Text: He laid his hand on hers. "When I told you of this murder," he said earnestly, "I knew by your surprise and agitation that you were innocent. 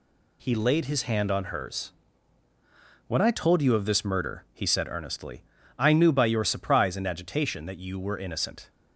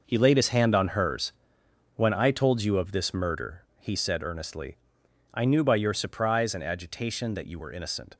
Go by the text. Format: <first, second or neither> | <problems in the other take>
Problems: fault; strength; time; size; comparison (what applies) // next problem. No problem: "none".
first | gets quieter; strong; throughout; 10.5 dB